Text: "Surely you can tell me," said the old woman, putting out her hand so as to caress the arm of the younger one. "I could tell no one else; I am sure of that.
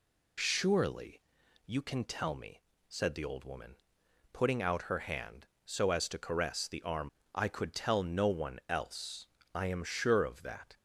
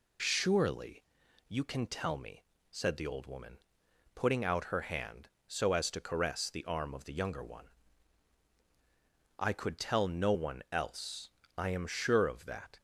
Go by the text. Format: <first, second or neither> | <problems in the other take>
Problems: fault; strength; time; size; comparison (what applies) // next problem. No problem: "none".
second | pauses between "Surely" and "you"; noticeable; at 1.2 s; 0.46 s long; noticeable in the second // skips "of the younger one"; at 7.2 s